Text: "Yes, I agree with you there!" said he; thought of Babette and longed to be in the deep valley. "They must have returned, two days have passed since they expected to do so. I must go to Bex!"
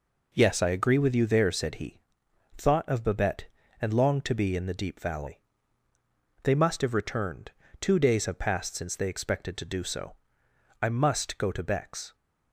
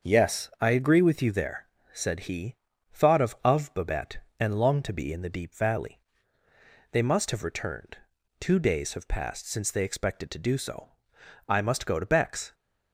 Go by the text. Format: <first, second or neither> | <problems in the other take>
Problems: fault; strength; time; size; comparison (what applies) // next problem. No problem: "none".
first | starts louder than the rest; until 1.1 s; 6.5 dB // says "of" twice; at 3.4 s